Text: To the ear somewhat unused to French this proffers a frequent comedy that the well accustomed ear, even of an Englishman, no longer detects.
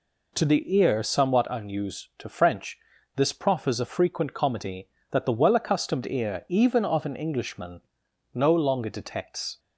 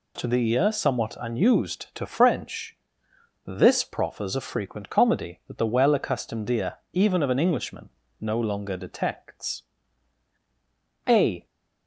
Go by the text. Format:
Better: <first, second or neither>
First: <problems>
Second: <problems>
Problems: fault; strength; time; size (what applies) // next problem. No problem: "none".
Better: first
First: pauses between "French" and "this"; at 2.7 s; 0.38 s long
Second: pauses between "French" and "this"; noticeable; at 2.7 s; 0.70 s long // goes on to say "A"; slight; from 11.0 s on; 0.40 s long